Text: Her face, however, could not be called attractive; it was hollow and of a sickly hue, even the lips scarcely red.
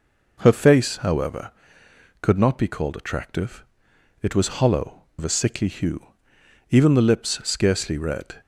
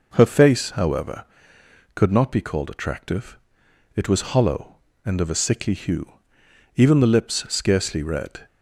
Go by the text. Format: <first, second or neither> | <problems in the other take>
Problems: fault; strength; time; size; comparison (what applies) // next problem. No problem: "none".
second | skips "and"; at 5.1 s